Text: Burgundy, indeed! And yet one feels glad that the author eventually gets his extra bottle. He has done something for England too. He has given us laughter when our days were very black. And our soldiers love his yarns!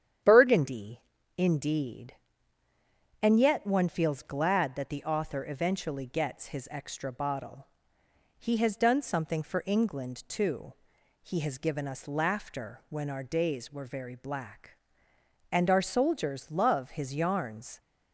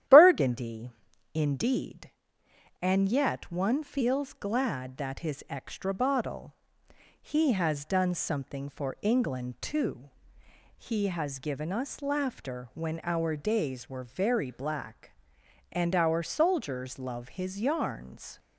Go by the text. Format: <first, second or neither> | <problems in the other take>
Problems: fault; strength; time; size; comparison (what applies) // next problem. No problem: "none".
first | starts louder than the rest; strong; until 1.5 s; 11.5 dB; strong in the first // skips "the author eventually gets"; at 5.1 s